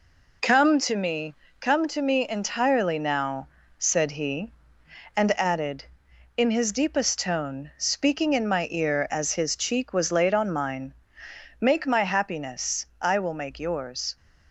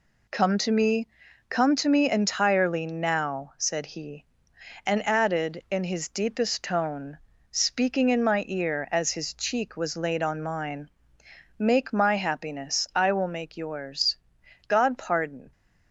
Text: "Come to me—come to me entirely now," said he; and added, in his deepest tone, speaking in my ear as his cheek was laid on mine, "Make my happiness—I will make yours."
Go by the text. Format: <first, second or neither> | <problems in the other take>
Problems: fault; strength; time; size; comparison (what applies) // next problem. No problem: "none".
first | goes on to say "God pardon"; noticeable; from 14.6 s on; 0.84 s long